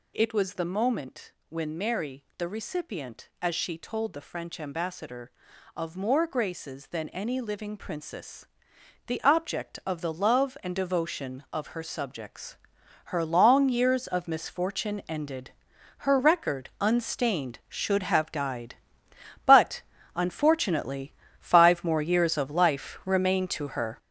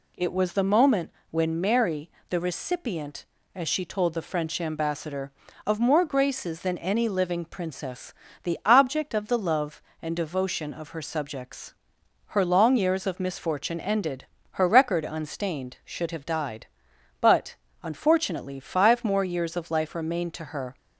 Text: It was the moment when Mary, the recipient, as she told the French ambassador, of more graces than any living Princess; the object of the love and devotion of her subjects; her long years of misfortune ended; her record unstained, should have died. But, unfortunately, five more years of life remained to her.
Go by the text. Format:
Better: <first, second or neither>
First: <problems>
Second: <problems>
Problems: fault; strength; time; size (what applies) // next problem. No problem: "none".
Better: second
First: gets louder; strong; throughout; 8 dB // pauses between "moment" and "when"; slight; at 1.3 s; 0.16 s long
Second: pauses between "moment" and "when"; slight; at 1.1 s; 0.20 s long